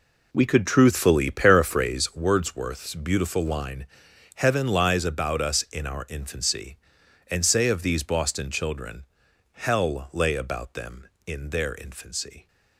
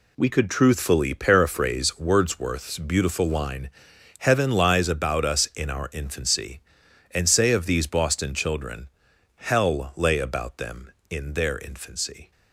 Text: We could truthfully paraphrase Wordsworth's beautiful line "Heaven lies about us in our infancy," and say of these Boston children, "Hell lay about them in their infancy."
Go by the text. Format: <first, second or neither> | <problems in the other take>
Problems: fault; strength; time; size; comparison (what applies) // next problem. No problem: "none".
second | starts louder than the rest; slight; until 2.0 s; 3.5 dB // pauses between "line" and "Heaven"; noticeable; at 3.8 s; 0.50 s long; noticeable in the second